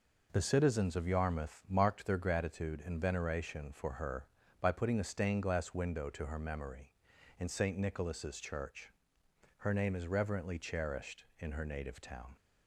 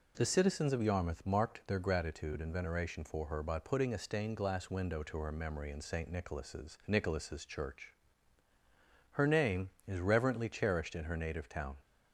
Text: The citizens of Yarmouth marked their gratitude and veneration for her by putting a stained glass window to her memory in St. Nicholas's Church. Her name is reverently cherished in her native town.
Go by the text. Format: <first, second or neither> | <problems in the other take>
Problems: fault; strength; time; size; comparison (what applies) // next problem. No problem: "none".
first | says "Nicholas's" twice; at 6.8 s